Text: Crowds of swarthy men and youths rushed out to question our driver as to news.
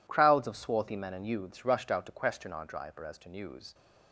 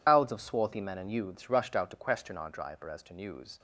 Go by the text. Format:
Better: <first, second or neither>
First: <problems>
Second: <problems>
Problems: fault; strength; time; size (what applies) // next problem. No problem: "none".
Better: first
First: none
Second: loses the start of "Crowds"; at 0.0 s; 140 ms